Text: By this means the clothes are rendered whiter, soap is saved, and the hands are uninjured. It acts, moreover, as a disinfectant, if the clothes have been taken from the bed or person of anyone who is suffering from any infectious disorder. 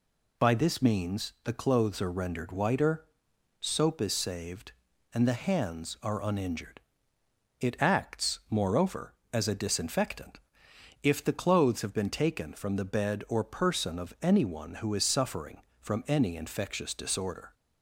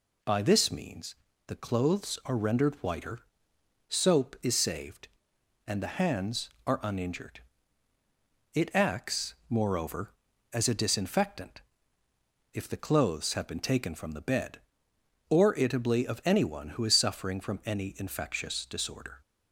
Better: first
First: none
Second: pauses between "means" and "the"; slight; at 1.1 s; 0.32 s long // says "itably" for "person"; at 15.5 s

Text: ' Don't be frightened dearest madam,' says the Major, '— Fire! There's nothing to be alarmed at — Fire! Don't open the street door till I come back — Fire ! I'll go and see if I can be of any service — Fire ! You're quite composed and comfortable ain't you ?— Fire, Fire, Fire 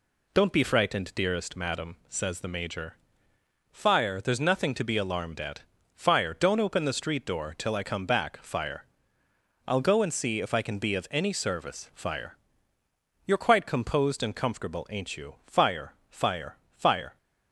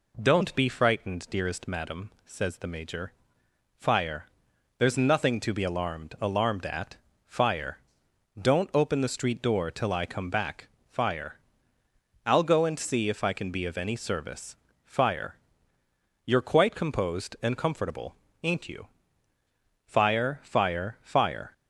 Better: first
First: none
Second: says "alarmed" twice; at 6.2 s // pauses between "comfortable" and "ain't"; slight; at 18.1 s; 0.27 s long

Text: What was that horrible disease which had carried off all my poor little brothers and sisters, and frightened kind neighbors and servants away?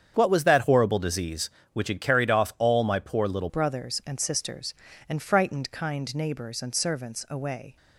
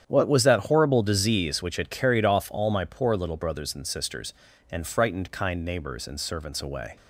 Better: second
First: starts louder than the rest; strong; until 1.1 s; 8 dB // changes voice at "brothers"; from 3.4 s on; 4.3 s long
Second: starts louder than the rest; strong; until 1.0 s; 9 dB

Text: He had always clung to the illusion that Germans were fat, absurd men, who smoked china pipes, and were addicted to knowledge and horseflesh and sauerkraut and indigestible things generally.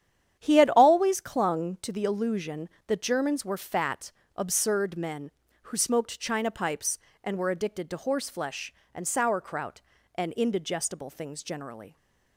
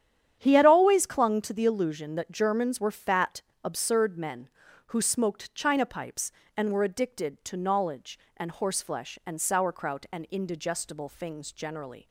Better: second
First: starts louder than the rest; strong; until 1.4 s; 9.5 dB // skips "knowledge and"; at 7.9 s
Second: starts louder than the rest; strong; until 1.4 s; 9.5 dB

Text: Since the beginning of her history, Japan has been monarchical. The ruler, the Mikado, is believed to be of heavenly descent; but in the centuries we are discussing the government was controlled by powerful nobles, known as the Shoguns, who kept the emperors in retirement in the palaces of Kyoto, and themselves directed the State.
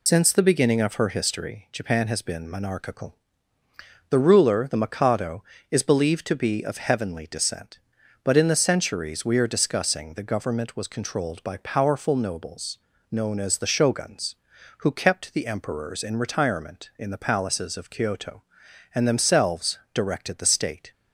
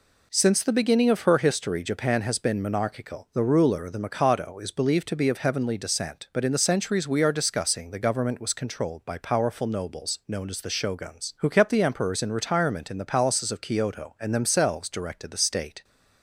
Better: second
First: loses the start of "Since"; at 0.0 s; 85 ms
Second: none

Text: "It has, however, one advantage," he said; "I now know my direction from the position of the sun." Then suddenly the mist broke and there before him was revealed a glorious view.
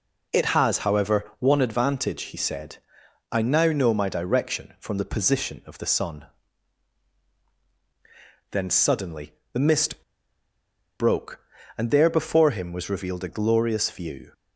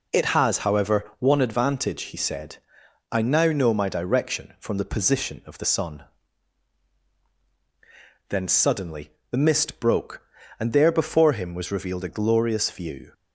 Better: second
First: pauses between "suddenly" and "the"; slight; at 9.3 s; 0.20 s long // pauses between "mist" and "broke"; noticeable; at 10.0 s; 0.97 s long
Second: pauses between "suddenly" and "the"; slight; at 9.1 s; 0.20 s long

